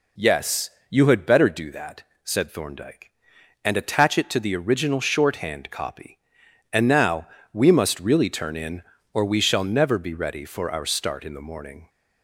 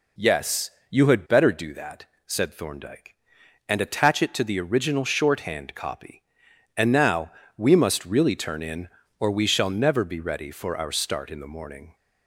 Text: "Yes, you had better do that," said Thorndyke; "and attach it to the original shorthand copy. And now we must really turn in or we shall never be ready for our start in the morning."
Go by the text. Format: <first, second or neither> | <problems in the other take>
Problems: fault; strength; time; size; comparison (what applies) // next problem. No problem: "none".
neither | pauses between "now" and "we"; slight; the same in both